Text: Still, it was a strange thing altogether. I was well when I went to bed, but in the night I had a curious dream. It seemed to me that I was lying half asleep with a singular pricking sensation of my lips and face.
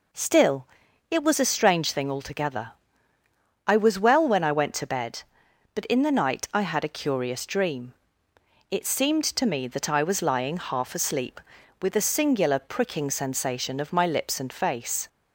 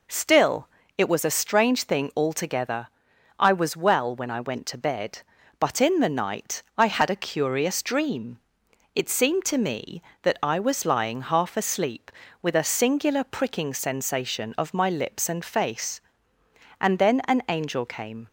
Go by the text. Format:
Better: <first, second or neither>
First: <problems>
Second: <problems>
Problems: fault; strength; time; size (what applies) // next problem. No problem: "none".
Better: first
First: none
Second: pauses between "night" and "I"; slight; at 6.6 s; 0.16 s long // goes on to say "And then an angel came"; from 16.8 s on; 1.4 s long